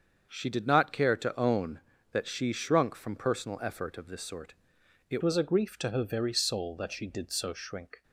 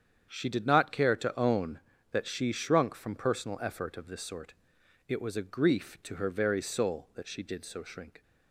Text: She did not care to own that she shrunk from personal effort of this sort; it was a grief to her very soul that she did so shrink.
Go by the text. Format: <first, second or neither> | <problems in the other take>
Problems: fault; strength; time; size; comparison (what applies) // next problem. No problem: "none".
second | starts louder than the rest; until 1.3 s; 7 dB; strong in the second // changes voice at "was"; from 5.2 s on; 2.8 s long